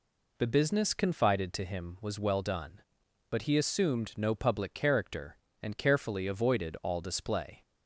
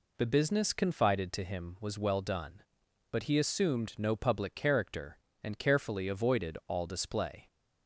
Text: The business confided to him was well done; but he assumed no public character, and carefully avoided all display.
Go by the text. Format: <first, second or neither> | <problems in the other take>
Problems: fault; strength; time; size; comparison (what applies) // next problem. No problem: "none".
neither | none